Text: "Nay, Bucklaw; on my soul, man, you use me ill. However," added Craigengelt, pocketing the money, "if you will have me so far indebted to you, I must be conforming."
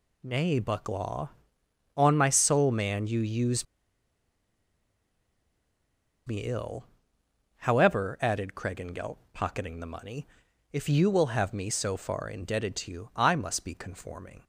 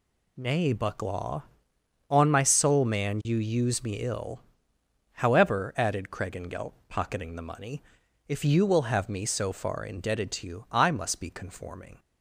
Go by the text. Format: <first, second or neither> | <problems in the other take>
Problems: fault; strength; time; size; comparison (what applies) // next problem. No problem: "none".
second | pauses between "use" and "me"; strong; at 3.6 s; 2.6 s long